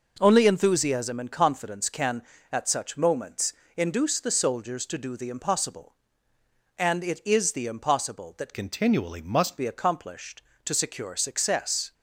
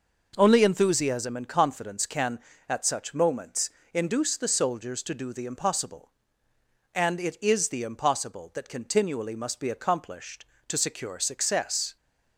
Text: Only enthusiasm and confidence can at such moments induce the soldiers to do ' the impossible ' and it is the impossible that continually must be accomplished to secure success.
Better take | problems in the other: second | pauses between "moments" and "induce"; slight; at 3.5 s; 0.22 s long; slight in the second // changes voice from "continually" to "must"; from 8.5 to 9.5 s; 1.0 s long

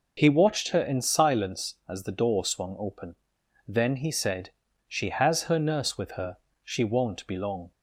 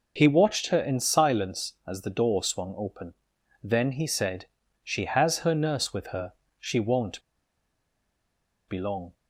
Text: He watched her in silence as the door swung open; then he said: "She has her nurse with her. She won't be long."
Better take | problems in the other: first | pauses between "won't" and "be"; strong; at 7.2 s; 1.4 s long

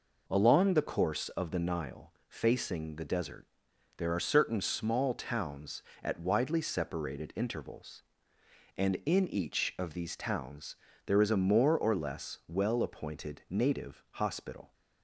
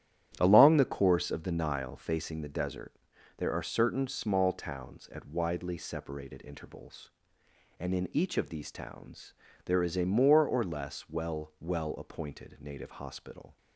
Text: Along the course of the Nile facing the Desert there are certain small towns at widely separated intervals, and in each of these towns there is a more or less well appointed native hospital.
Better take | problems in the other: first | starts louder than the rest; strong; until 1.3 s; 11 dB // pauses between "Desert" and "there"; at 2.9 s; 0.42 s long; noticeable in the first // pauses between "towns" and "there"; slight; at 9.3 s; 0.32 s long; slight in the first // says "well" twice; at 11.5 s

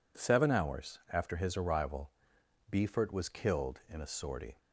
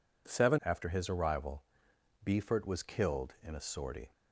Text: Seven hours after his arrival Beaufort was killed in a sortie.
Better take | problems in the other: first | skips "hours"; at 0.6 s // pauses between "arrival" and "Beaufort"; noticeable; at 1.6 s; 0.62 s long; noticeable in the first

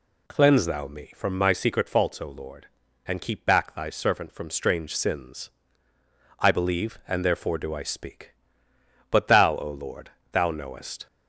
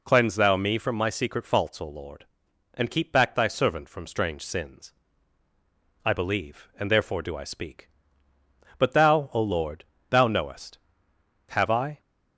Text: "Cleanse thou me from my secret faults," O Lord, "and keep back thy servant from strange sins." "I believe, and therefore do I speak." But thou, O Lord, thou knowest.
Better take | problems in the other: first | goes on to say "Have I"; from 11.4 s on; 0.50 s long

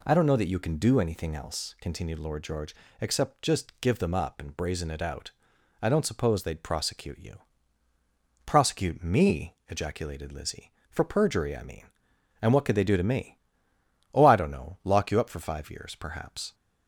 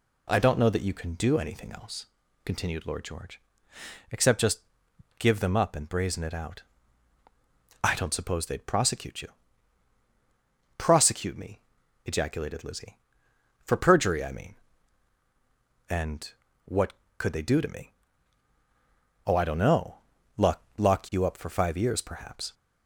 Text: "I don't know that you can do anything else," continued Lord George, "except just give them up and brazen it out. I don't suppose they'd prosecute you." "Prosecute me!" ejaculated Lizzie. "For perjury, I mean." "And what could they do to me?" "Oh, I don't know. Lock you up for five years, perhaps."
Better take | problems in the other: first | pauses between "just" and "give"; noticeable; at 4.6 s; 0.58 s long // pauses between "And" and "what"; slight; at 16.3 s; 0.34 s long // says "Lock" twice; at 20.7 s

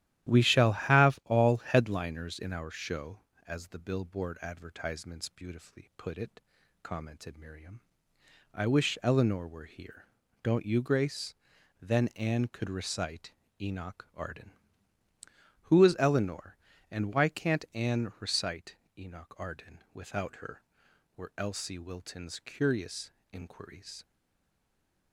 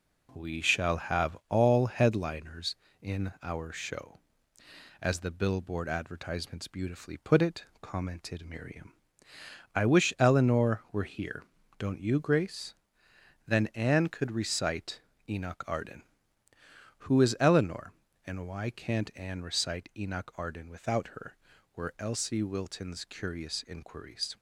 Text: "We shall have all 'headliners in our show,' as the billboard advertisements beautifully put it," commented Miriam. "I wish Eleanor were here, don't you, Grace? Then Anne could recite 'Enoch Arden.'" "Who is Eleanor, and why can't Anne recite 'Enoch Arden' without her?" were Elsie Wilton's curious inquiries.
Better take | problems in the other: second | starts louder than the rest; strong; until 1.3 s; 12.5 dB // pauses between "recite" and "Enoch"; slight; at 13.3 s; 0.26 s long; slight in the second // pauses between "recite" and "Enoch"; slight; at 18.7 s; 0.20 s long // pauses between "curious" and "inquiries"; slight; at 23.0 s; 0.22 s long // stays silent after the last word; from 24.0 s on; 1.1 s long

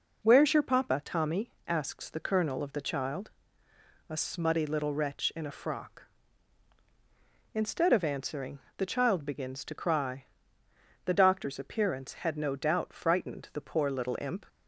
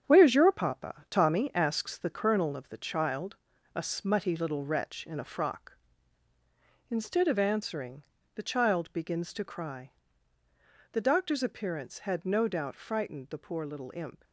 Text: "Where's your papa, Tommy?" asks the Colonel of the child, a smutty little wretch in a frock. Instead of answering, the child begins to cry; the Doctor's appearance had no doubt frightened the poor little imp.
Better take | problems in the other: first | gets quieter; throughout; 7 dB

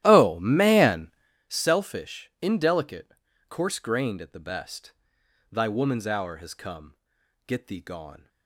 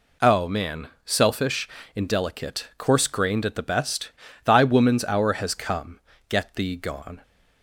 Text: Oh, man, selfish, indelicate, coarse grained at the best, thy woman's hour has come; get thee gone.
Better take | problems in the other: second | starts louder than the rest; strong; until 1.3 s; 13.5 dB

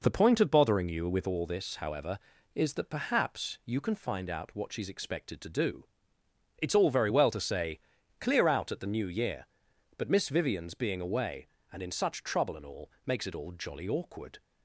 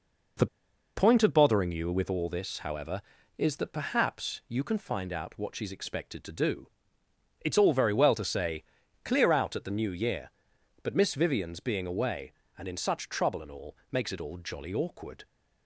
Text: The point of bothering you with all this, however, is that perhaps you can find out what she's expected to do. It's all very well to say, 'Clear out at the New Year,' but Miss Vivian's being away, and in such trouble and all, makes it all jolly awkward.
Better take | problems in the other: first | pauses between "The" and "point"; noticeable; at 0.4 s; 0.50 s long

